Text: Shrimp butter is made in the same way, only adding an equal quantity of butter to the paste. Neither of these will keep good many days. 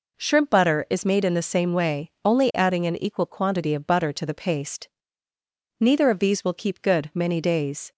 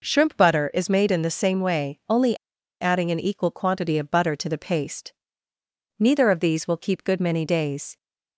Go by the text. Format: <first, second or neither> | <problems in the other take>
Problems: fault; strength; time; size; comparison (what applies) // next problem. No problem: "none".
first | pauses between "only" and "adding"; at 2.3 s; 0.45 s long